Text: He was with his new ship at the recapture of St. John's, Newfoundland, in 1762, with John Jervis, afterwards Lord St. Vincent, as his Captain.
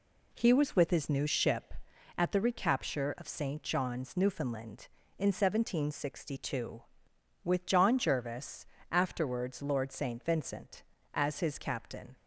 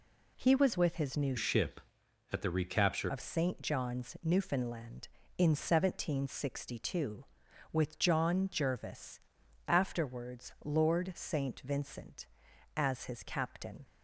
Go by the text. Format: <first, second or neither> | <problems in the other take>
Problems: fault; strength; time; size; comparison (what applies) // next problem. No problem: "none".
first | changes voice from "ship" to "recapture"; from 1.3 to 3.0 s; 1.7 s long